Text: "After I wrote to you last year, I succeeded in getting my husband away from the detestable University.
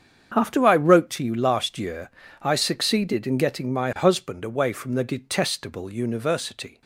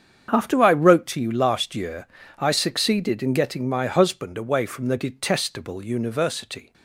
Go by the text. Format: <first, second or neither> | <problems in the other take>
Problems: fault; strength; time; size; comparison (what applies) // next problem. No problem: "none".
neither | starts louder than the rest; strong; the same in both